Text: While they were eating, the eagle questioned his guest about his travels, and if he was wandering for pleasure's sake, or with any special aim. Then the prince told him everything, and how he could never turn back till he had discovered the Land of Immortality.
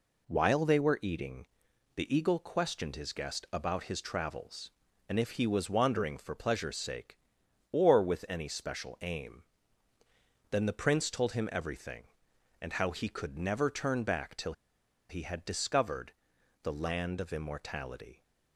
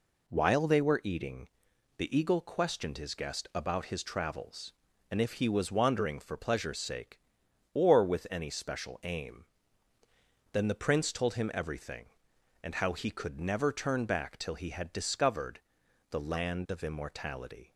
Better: second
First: pauses between "till" and "he"; noticeable; at 14.5 s; 0.56 s long // pauses between "discovered" and "the"; noticeable; at 16.1 s; 0.50 s long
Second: pauses between "discovered" and "the"; noticeable; at 15.6 s; 0.50 s long

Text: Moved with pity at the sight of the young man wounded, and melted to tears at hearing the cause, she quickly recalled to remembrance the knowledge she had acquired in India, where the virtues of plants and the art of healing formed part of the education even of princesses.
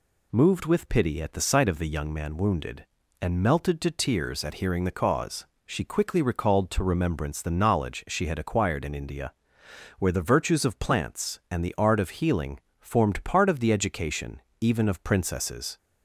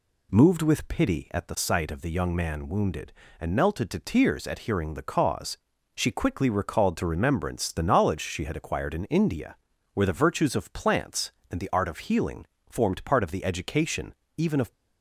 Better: first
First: pauses between "healing" and "formed"; slight; at 12.5 s; 0.20 s long // pauses between "education" and "even"; slight; at 14.4 s; 0.20 s long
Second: pauses between "healing" and "formed"; slight; at 12.4 s; 0.22 s long // pauses between "education" and "even"; slight; at 14.1 s; 0.22 s long // stops before "princesses"; at 14.7 s

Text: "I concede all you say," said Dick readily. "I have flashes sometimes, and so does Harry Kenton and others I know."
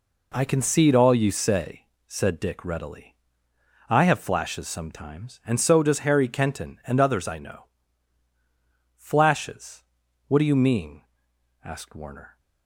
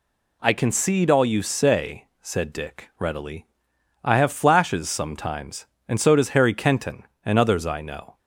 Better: second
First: goes on to say "Flashes What do you mean asked Warner"; strong; from 8.9 s on; 3.4 s long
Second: none

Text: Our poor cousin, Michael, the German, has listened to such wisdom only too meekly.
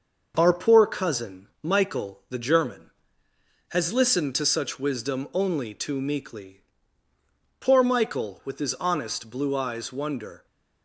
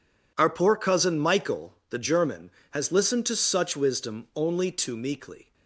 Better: second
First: starts louder than the rest; noticeable; until 1.3 s; 6 dB // goes on to say "Poor Michael with his honest blue eyes wonder"; strong; from 7.6 s on; 2.8 s long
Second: none

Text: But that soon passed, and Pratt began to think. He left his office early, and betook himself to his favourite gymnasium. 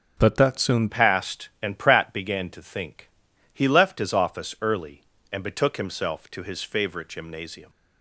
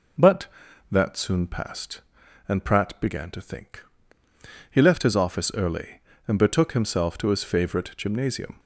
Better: second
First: changes voice at "passed"; from 0.8 s on; 6.8 s long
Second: none

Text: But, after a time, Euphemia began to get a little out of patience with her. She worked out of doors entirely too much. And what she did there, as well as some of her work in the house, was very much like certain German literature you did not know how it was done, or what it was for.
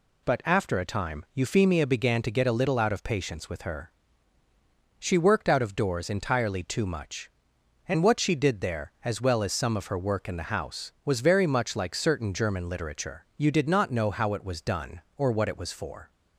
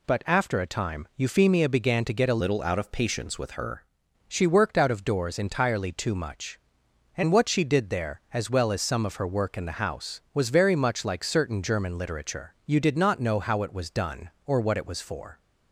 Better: first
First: none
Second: changes voice from "little" to "her"; from 2.3 to 3.8 s; 1.5 s long

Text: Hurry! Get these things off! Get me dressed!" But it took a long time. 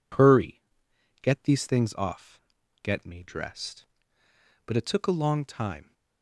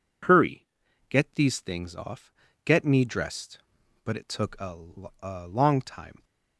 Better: first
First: none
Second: says "a" twice; at 5.2 s

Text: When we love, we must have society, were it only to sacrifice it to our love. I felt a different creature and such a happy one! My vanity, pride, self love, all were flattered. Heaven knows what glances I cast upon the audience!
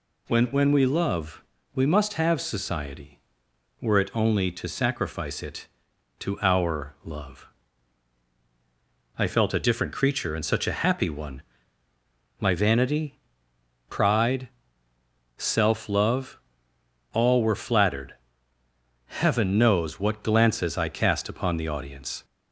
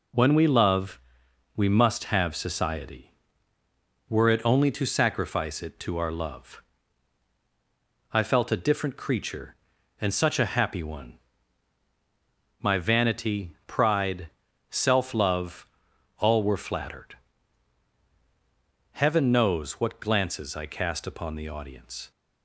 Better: second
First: says "When" twice; at 0.4 s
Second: none

